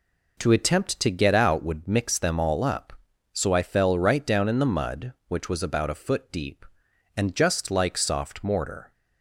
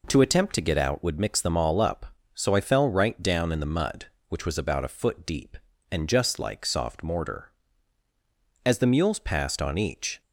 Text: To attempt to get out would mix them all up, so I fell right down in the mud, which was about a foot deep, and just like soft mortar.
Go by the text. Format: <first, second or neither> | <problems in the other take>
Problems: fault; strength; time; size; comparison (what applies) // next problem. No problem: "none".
first | goes on to say "As the mules passed on each"; from 8.6 s on; 1.5 s long